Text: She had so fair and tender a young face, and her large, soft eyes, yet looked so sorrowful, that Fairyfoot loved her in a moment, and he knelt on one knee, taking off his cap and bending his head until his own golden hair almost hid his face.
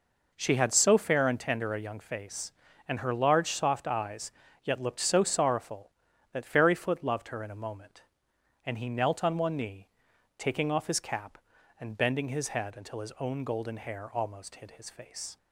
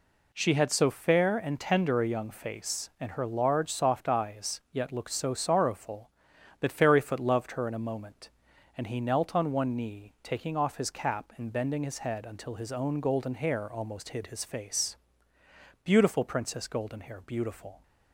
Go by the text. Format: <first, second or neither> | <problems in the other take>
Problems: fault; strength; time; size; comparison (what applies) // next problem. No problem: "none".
first | goes on to say "Beautiful Princess Goldenhair beautiful"; strong; from 15.8 s on; 1.9 s long